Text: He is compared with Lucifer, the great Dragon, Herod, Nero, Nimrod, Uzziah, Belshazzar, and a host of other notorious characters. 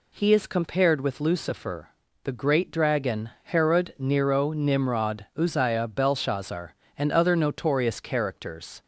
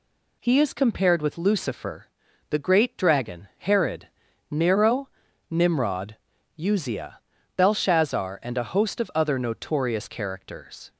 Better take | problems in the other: second | skips "a host of"; at 7.1 s

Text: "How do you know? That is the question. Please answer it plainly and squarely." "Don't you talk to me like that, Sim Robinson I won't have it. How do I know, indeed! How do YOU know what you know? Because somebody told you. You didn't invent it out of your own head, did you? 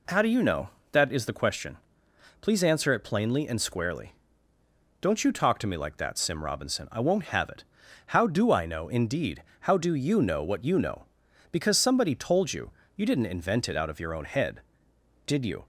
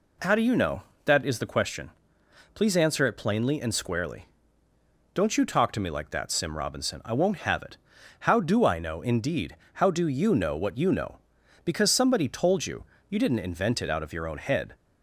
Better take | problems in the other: first | stops before "did you"; at 14.7 s

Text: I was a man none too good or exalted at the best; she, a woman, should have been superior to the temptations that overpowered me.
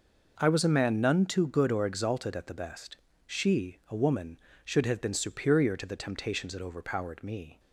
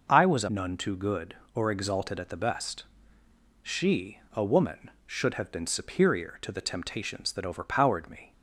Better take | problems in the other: first | skips "man"; at 0.4 s

